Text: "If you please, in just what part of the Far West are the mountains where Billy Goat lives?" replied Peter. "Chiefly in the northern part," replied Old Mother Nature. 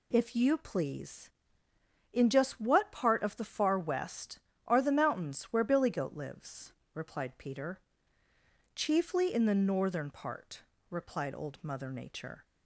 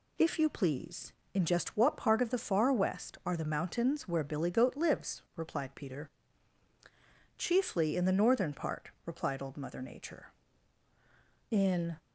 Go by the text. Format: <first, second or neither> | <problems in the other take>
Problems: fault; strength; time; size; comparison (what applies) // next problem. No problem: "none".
first | goes on to say "In"; slight; from 11.5 s on; 0.46 s long